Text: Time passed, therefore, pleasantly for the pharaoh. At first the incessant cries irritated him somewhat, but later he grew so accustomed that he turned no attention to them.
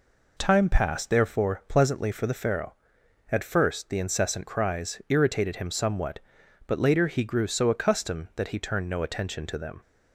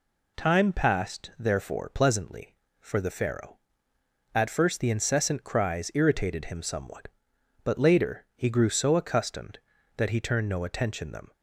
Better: first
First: none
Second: skips "to"; at 11.1 s

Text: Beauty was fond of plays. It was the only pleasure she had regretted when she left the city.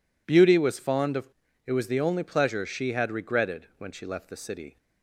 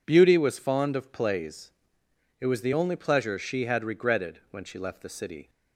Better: second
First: skips "plays"; at 1.4 s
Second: none

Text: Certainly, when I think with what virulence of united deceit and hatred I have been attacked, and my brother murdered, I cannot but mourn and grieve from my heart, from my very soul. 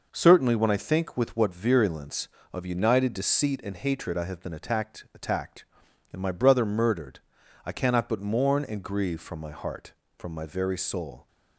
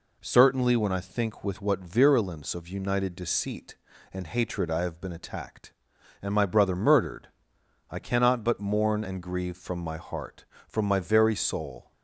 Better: second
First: says "attacked" twice; at 5.1 s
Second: none

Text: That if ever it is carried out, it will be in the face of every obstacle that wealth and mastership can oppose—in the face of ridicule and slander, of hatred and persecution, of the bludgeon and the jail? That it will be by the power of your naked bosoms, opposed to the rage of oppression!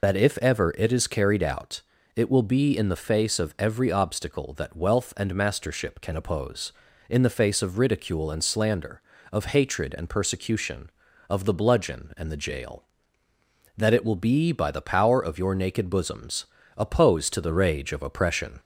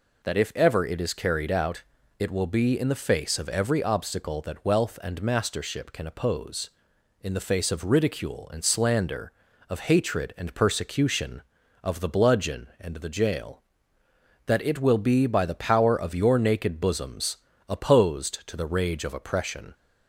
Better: second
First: loses the start of "That"; at 0.0 s; 55 ms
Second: none

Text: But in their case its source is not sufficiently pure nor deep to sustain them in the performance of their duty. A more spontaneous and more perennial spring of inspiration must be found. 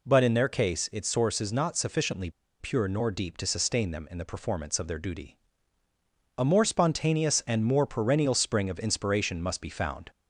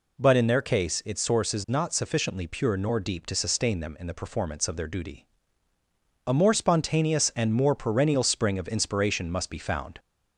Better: second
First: pauses between "sufficiently" and "pure"; slight; at 2.3 s; 0.30 s long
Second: none

